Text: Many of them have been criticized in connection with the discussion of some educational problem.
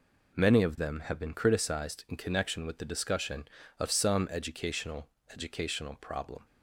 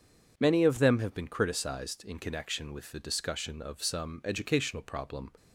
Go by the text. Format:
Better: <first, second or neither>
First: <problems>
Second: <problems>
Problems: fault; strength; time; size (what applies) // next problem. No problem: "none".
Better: second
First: says "educational" twice; at 5.3 s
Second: none